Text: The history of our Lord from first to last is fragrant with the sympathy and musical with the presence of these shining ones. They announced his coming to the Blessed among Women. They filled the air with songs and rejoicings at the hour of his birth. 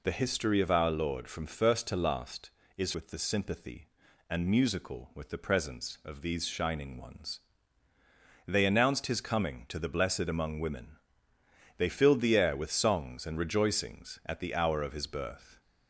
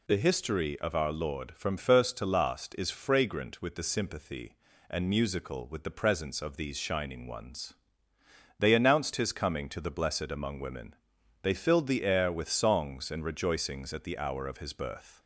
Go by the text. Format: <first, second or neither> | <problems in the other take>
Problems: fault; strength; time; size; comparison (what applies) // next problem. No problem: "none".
second | skips "fragrant"; at 2.9 s